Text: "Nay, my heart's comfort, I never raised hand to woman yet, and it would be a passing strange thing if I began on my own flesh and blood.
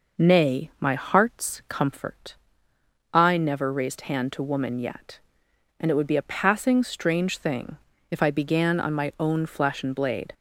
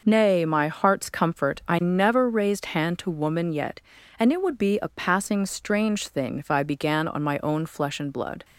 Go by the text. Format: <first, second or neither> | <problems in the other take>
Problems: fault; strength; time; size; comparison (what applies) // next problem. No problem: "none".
second | pauses between "thing" and "if"; slight; at 7.7 s; 0.32 s long // says "blade" for "blood"; at 9.9 s